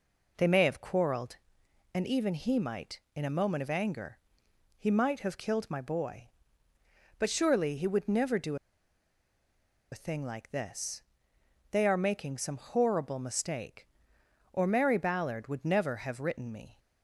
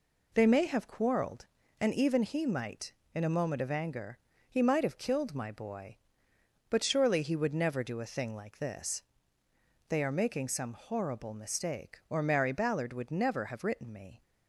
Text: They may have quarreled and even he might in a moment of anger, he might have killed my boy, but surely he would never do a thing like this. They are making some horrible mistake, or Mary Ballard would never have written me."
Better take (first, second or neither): second